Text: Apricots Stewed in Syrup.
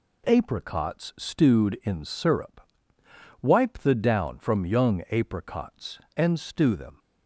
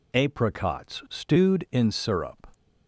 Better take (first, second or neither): second